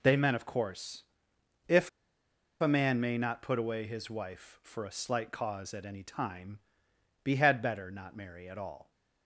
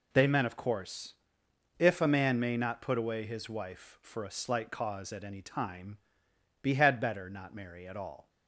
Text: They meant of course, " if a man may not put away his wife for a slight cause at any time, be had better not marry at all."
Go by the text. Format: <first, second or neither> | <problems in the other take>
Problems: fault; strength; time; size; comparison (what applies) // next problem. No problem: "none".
second | pauses between "if" and "a"; noticeable; at 1.8 s; 0.71 s long